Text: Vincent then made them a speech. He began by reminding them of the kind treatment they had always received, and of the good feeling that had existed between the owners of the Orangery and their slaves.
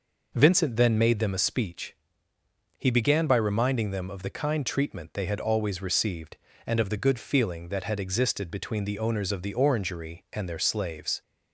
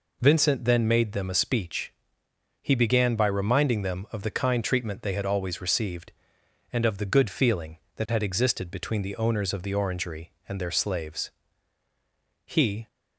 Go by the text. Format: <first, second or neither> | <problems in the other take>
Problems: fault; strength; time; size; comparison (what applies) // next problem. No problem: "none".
first | goes on to say "He"; slight; from 12.4 s on; 0.42 s long